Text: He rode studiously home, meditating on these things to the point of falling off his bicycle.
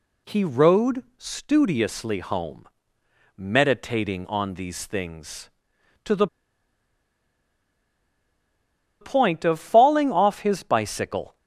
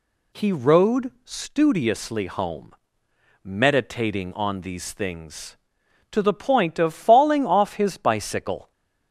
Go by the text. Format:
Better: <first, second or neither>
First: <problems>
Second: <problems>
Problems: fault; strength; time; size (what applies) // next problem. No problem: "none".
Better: second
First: pauses between "the" and "point"; strong; at 6.2 s; 2.7 s long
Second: none